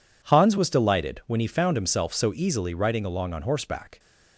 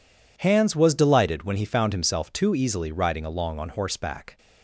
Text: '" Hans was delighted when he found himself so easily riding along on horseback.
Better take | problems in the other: first | says "too" for "so"; at 2.3 s

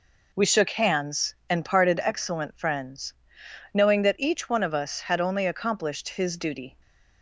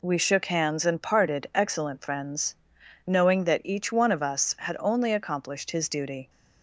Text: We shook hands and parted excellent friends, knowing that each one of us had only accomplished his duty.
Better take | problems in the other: neither | none

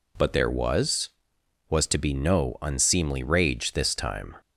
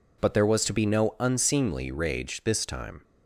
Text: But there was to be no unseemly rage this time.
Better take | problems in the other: second | says "was" twice; at 1.6 s

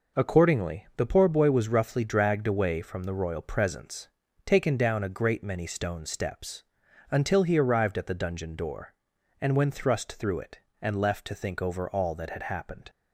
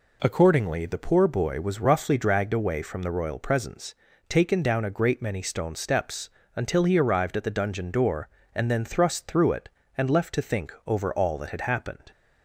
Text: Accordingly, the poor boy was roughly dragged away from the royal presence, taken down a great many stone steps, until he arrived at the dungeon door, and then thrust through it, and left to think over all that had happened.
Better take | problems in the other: second | says "when" for "then"; at 9.5 s

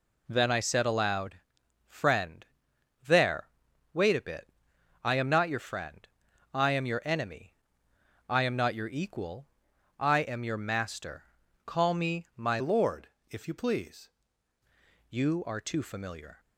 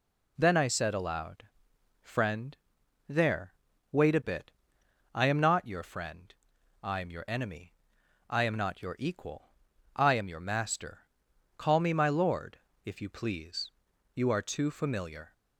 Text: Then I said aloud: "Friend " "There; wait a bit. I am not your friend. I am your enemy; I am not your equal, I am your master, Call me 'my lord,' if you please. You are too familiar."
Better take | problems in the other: second | changes voice from "lord" to "please"; from 12.5 to 14.1 s; 1.6 s long

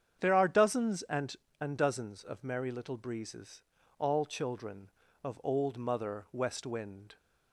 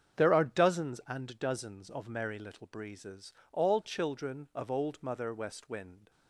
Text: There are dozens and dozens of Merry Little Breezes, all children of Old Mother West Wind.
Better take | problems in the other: second | starts louder than the rest; strong; until 1.2 s; 8.5 dB; strong in the second // says "and" twice; at 1.6 s

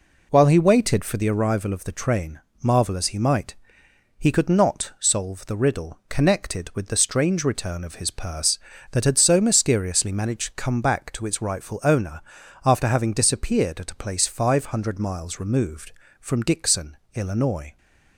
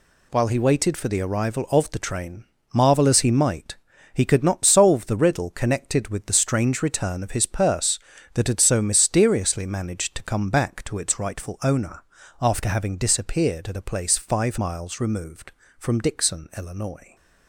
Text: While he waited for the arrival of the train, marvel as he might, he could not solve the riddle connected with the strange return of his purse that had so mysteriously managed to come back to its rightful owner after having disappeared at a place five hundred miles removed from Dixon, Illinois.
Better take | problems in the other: first | pauses between "owner" and "after"; at 12.0 s; 0.40 s long; also in the first // skips "hundred"; at 14.5 s

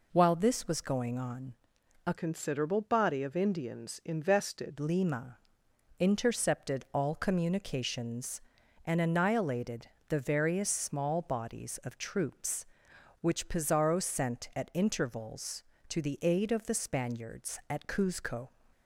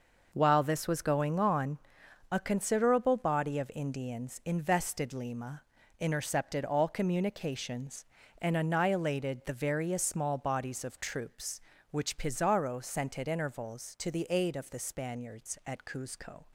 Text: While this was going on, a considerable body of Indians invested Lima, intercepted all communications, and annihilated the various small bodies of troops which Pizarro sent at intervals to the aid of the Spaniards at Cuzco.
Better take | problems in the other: second | changes voice from "considerable" to "invested"; from 2.1 to 4.7 s; 2.6 s long // pauses between "annihilated" and "the"; slight; at 9.8 s; 0.20 s long

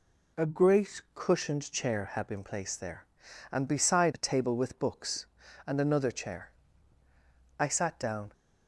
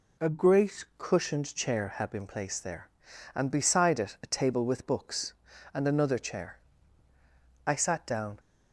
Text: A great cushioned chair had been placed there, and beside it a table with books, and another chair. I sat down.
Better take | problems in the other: second | skips "it"; at 4.1 s

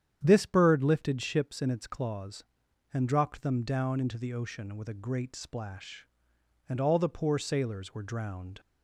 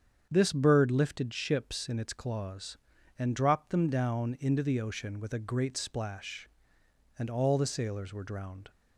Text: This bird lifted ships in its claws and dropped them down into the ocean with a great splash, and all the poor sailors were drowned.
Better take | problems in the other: first | starts louder than the rest; strong; until 1.3 s; 7.5 dB; strong in the first // skips "poor"; at 7.6 s

